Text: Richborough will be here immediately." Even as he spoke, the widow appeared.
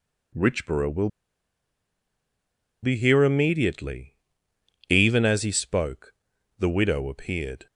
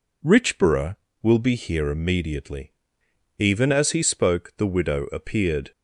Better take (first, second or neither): second